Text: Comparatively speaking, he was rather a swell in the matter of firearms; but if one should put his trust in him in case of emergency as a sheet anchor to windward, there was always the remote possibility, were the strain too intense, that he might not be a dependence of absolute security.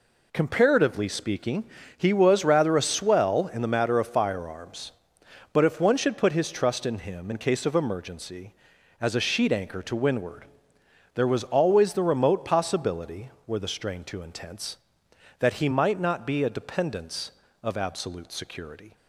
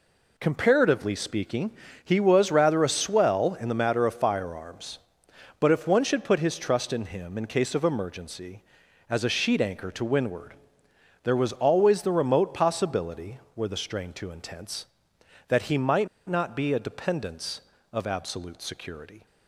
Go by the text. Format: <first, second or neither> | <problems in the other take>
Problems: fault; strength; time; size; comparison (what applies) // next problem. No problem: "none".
first | pauses between "might" and "not"; slight; at 16.0 s; 0.21 s long